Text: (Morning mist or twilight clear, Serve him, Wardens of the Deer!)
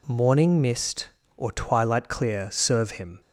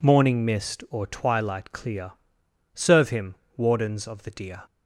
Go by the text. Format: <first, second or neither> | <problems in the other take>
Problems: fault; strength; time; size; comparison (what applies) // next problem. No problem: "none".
second | stops before "Wardens of the Deer"; at 3.2 s